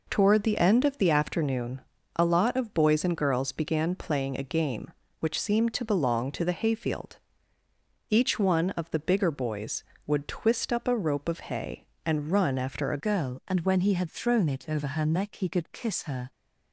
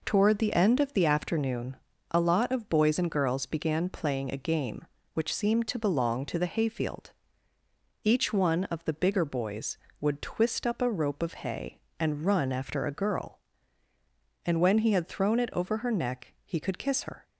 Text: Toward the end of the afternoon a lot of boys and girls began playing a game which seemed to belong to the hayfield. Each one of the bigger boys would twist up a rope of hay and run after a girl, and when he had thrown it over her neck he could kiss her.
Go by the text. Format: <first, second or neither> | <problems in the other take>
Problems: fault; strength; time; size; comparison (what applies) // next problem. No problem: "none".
second | pauses between "afternoon" and "a"; slight; at 1.8 s; 0.34 s long; slight in the second // changes voice at "girl"; from 13.0 s on; 3.3 s long